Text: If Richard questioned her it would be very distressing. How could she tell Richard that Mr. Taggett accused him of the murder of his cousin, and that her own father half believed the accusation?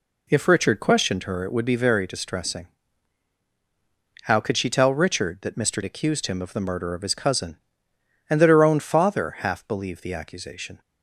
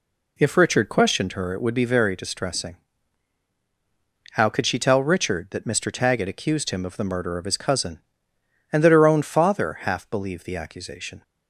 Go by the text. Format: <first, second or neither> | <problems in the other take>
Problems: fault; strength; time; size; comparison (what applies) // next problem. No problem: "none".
second | skips "Taggett"; at 5.8 s